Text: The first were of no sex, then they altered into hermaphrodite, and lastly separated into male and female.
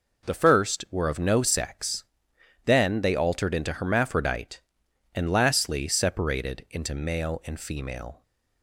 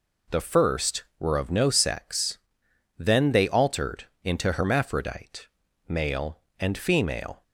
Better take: first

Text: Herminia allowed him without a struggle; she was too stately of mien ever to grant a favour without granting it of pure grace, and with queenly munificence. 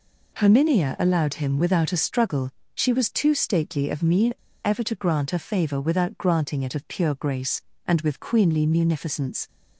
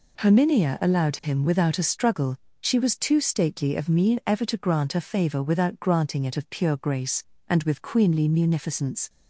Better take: second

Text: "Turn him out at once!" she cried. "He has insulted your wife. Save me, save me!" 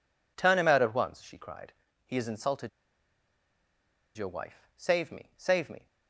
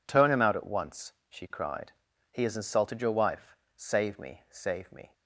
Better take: second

